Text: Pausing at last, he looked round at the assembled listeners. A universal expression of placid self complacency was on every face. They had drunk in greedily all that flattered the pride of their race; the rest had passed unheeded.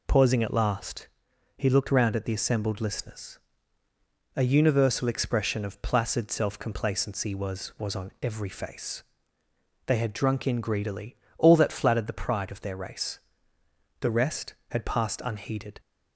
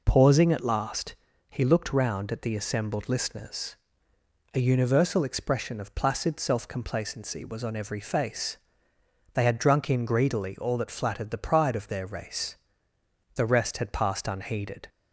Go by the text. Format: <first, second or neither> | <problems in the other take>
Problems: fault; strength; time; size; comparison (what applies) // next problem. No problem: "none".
second | says "was" twice; at 7.7 s // pauses between "greedily" and "all"; slight; at 11.1 s; 0.22 s long